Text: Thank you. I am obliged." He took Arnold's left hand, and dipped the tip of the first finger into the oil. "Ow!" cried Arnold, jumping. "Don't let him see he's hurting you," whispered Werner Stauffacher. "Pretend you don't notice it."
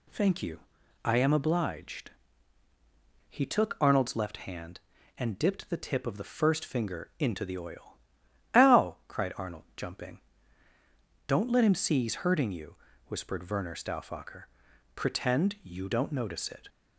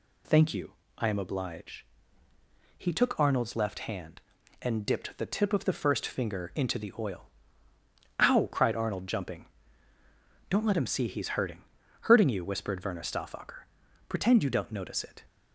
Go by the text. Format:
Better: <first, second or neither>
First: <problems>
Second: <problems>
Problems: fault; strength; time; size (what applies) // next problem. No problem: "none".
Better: first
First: none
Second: says "hurting" twice; at 12.0 s